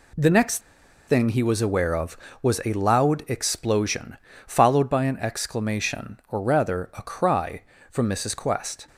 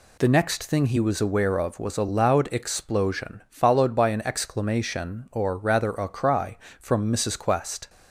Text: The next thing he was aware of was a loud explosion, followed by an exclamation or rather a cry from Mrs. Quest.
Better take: second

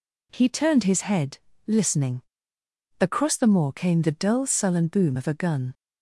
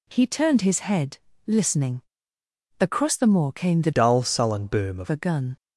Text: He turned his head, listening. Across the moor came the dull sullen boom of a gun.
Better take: first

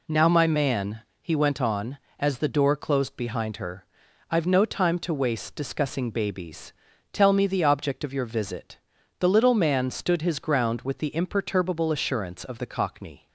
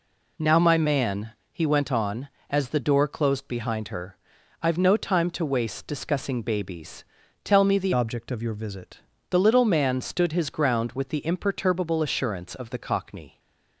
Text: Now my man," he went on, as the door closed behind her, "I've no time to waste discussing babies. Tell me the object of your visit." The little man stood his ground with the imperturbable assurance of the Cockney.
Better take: first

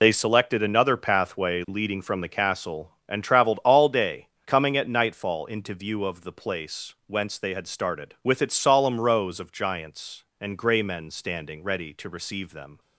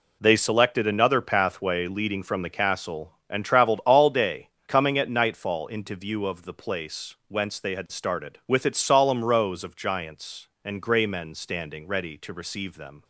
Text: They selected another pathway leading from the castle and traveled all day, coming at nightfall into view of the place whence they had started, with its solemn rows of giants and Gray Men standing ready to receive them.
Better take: second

